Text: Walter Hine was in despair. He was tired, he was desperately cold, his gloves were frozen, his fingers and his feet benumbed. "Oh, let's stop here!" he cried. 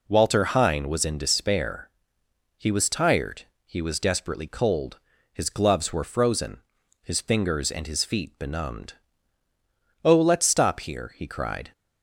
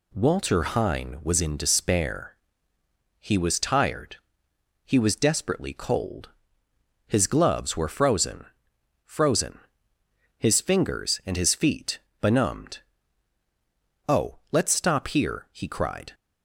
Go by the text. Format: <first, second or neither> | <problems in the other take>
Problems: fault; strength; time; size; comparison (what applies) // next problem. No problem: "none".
first | says "frozen" twice; at 9.0 s // pauses between "feet" and "benumbed"; slight; at 11.9 s; 0.24 s long